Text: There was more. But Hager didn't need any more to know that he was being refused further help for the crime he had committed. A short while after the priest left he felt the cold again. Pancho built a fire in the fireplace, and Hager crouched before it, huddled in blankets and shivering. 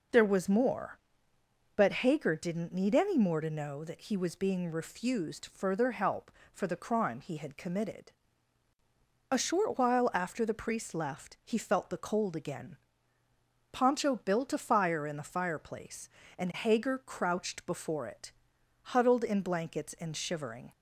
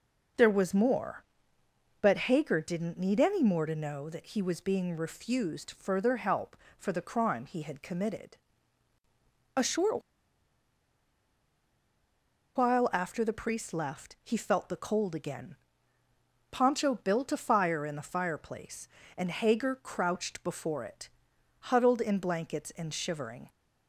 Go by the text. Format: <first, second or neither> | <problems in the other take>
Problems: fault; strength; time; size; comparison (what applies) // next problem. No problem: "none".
first | pauses between "short" and "while"; strong; at 10.0 s; 2.5 s long